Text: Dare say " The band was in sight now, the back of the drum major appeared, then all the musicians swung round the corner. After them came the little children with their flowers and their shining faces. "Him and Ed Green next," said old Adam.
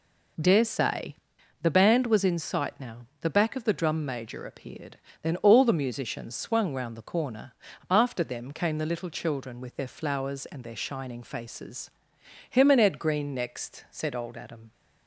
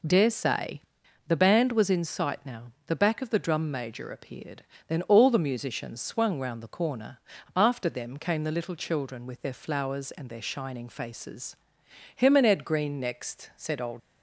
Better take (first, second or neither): first